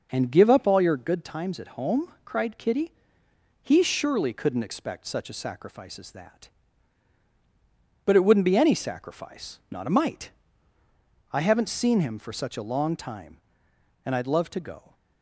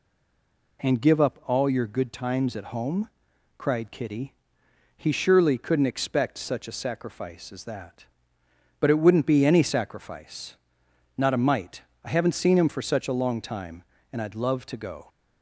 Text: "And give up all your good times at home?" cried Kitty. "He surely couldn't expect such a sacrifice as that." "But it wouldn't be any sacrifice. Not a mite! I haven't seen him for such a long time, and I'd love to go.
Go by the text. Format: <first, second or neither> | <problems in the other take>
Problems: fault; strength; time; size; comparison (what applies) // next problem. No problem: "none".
first | stays silent before the first word; slight; until 0.7 s; 0.7 s long